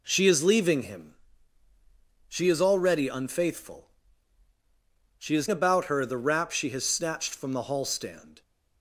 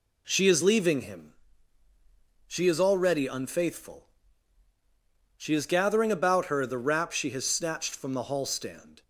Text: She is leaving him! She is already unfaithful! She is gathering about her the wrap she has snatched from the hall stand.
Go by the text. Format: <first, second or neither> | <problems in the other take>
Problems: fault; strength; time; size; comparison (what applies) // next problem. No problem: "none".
second | skips "gathering"; at 5.4 s